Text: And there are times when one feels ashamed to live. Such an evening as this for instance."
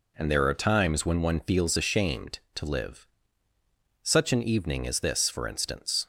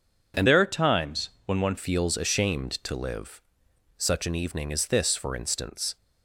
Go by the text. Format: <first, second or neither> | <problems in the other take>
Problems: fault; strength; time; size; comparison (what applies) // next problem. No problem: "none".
first | changes voice from "there" to "one"; from 0.4 to 1.7 s; 1.3 s long // pauses between "times" and "when"; slight; at 1.2 s; 0.16 s long